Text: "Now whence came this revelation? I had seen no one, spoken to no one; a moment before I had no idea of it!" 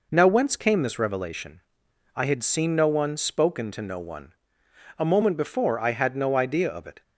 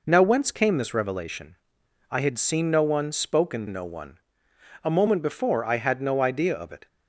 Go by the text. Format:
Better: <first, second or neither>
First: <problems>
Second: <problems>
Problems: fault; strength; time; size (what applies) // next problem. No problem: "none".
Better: first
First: none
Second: skips "to"; at 3.6 s